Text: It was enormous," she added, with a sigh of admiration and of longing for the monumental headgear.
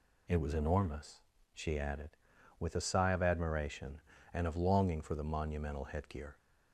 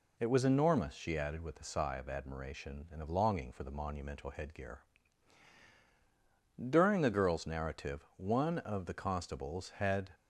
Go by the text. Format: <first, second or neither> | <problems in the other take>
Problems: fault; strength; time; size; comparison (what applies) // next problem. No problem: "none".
first | goes on to say "During the girl's narrative one of the constables had"; strong; from 6.5 s on; 3.5 s long